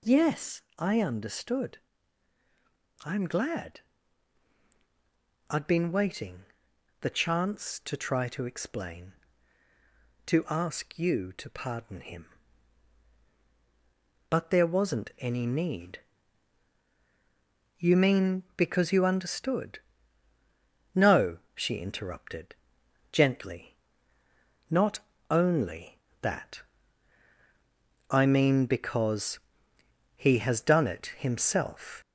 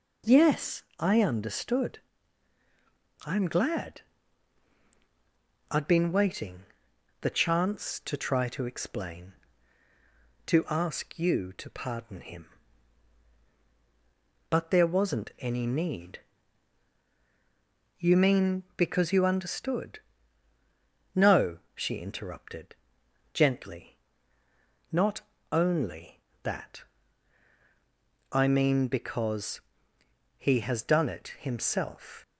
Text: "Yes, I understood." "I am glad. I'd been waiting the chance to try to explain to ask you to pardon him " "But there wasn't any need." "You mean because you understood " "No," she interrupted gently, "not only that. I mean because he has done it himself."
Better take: second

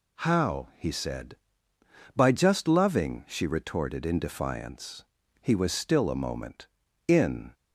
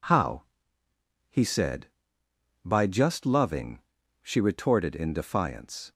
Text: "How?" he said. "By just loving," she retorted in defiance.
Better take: second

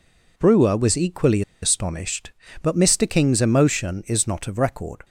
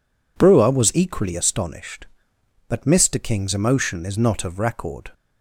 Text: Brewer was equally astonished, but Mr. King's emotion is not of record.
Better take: second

